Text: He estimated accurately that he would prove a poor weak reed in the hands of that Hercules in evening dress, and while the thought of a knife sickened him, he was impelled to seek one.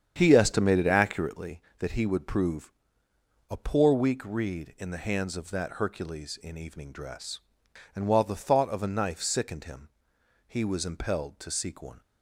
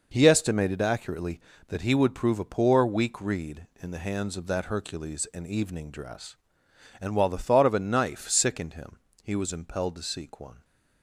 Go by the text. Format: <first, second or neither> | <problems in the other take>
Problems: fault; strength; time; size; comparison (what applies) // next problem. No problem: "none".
second | starts louder than the rest; strong; until 1.4 s; 8 dB // pauses between "prove" and "a"; noticeable; at 2.7 s; 0.78 s long